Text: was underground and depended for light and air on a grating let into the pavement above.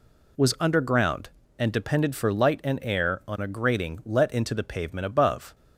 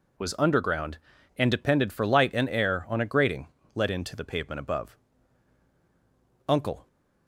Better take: first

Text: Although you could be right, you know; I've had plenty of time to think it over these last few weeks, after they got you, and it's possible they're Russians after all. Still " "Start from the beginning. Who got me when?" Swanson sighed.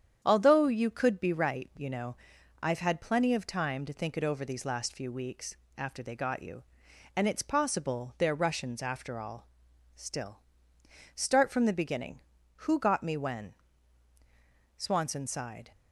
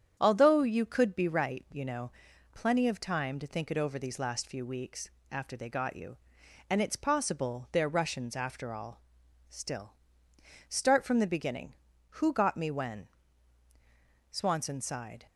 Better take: first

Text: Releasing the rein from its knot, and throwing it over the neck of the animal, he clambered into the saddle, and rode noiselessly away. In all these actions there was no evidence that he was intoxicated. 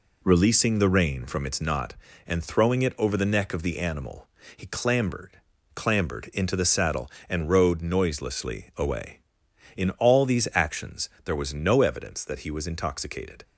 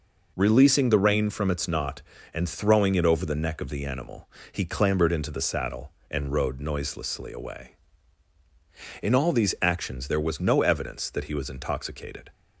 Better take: second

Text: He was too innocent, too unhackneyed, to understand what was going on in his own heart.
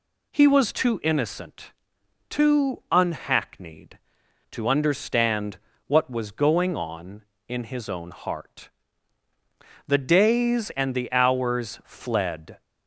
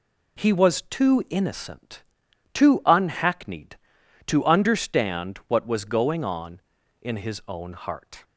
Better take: second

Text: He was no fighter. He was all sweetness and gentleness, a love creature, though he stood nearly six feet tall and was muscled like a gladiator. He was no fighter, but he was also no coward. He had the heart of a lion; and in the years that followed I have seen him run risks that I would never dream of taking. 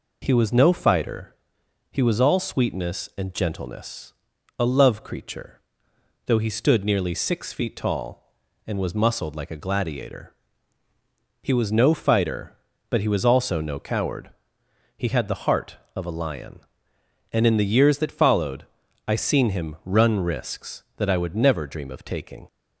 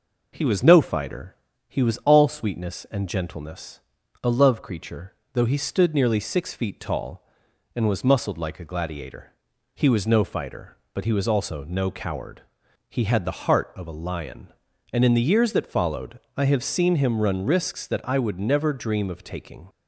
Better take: second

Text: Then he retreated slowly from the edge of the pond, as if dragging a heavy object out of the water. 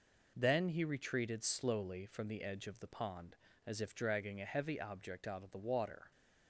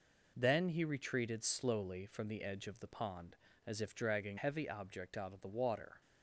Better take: first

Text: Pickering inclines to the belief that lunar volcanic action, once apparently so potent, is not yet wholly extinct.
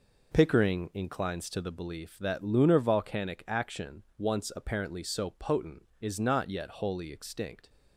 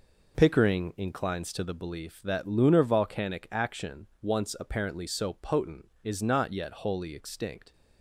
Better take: neither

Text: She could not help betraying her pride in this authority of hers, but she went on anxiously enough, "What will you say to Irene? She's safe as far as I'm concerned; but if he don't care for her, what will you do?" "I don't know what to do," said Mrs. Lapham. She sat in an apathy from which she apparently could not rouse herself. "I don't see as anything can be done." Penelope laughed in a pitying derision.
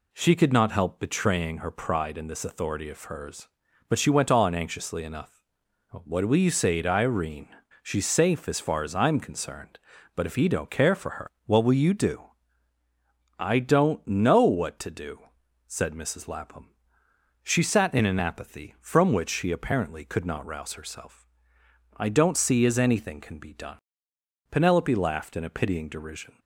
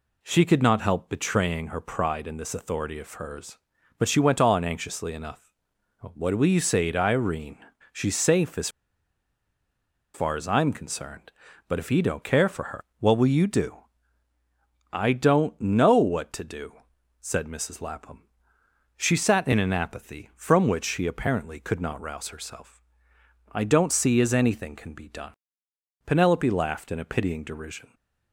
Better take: first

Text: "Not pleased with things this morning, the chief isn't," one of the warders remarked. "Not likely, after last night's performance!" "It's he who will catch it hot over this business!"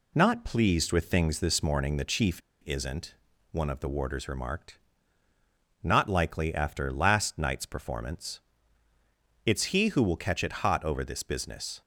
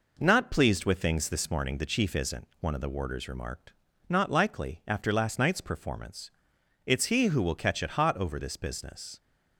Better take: second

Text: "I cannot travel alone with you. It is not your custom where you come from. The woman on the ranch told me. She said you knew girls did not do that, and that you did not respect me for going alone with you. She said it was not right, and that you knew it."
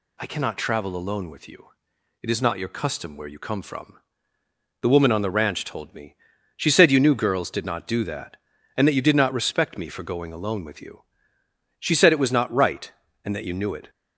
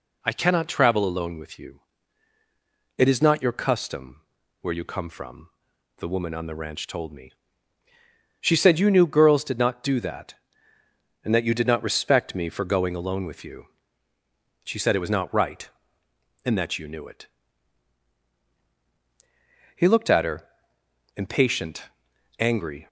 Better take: first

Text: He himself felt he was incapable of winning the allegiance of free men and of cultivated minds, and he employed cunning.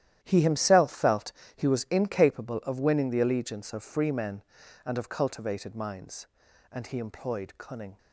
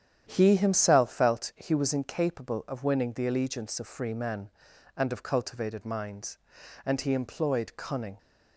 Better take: second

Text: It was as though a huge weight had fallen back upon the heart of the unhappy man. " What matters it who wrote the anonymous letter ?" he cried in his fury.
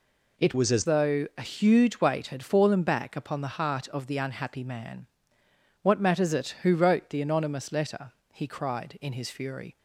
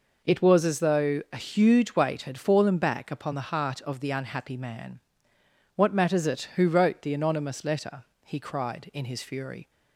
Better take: second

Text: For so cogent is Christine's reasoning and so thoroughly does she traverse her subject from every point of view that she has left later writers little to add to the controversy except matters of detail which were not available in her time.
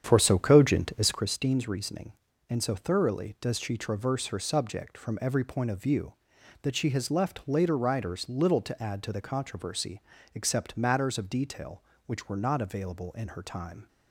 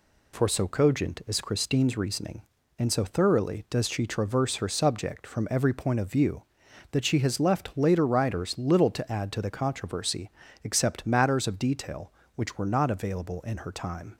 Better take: second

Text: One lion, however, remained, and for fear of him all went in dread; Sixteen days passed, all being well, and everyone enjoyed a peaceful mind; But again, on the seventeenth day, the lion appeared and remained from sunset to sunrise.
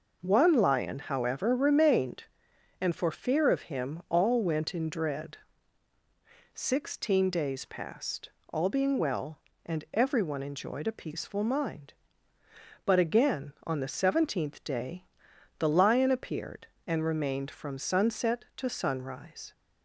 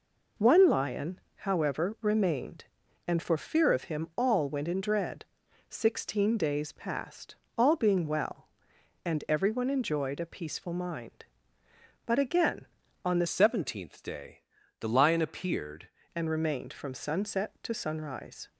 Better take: first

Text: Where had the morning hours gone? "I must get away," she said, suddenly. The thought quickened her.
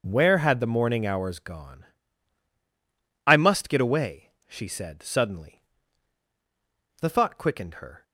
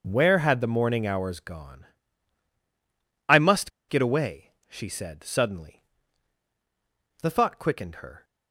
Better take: first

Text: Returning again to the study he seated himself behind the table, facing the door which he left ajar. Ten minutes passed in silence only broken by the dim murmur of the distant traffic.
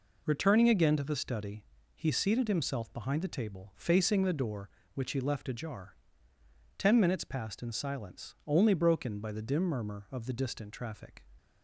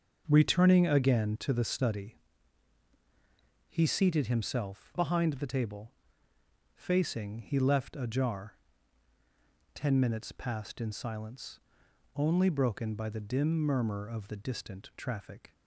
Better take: first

